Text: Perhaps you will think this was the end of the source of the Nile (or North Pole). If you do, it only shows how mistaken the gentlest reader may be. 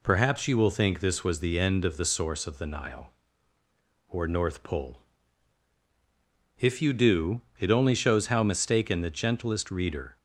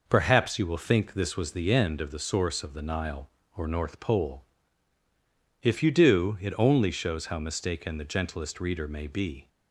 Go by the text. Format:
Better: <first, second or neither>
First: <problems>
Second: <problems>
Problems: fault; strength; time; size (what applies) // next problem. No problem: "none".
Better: second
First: stops before "may be"; at 10.1 s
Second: none